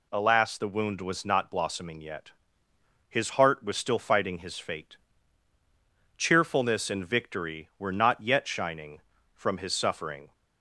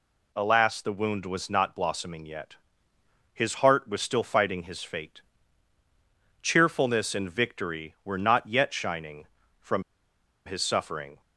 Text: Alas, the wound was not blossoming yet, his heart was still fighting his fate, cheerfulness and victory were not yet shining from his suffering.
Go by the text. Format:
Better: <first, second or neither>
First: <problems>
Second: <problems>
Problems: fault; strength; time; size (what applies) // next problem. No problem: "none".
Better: first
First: none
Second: pauses between "from" and "his"; noticeable; at 9.8 s; 0.64 s long